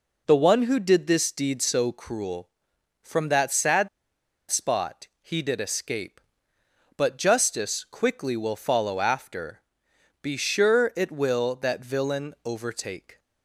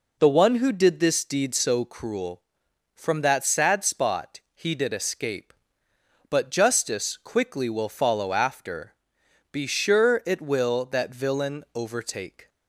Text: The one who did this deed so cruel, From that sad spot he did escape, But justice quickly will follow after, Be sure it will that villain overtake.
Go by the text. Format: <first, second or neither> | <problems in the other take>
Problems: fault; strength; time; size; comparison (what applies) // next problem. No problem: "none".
second | pauses between "sad" and "spot"; noticeable; at 3.8 s; 0.62 s long // pauses between "spot" and "he"; slight; at 5.0 s; 0.16 s long; slight in the second